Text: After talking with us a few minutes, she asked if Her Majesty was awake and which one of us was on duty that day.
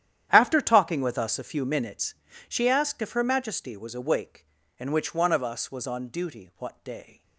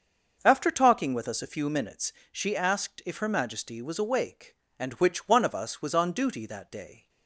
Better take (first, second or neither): second